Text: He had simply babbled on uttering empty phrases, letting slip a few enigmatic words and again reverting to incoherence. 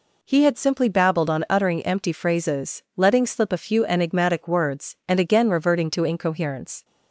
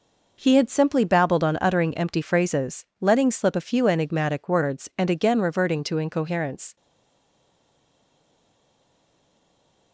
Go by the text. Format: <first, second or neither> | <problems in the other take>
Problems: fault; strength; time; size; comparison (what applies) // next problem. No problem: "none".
first | stays silent after the last word; strong; from 6.7 s on; 3.2 s long